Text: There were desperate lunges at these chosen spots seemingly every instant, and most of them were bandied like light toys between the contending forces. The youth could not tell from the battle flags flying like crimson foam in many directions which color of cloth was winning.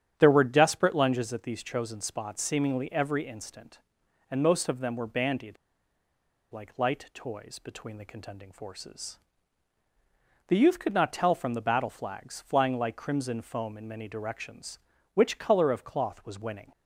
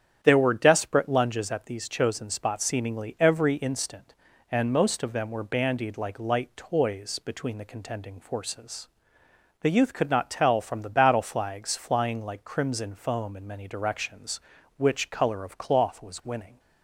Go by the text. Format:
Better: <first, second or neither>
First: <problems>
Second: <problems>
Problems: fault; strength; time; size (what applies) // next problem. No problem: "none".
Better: second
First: starts louder than the rest; strong; until 1.1 s; 10 dB // pauses between "bandied" and "like"; noticeable; at 5.5 s; 0.96 s long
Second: starts louder than the rest; strong; until 1.2 s; 9.5 dB